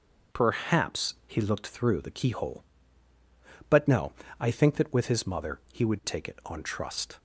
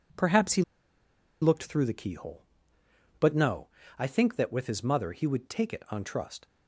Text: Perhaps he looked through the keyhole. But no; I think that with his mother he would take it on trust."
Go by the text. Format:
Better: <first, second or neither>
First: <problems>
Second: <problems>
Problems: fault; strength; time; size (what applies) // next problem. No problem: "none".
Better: first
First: none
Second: pauses between "he" and "looked"; noticeable; at 0.6 s; 0.78 s long